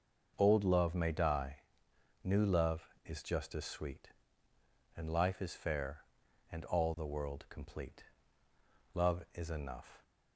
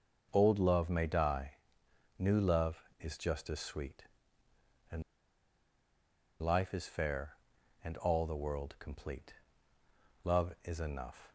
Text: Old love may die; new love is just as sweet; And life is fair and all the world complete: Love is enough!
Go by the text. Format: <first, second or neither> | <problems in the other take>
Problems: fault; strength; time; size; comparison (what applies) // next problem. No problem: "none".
first | pauses between "And" and "life"; strong; at 5.0 s; 1.3 s long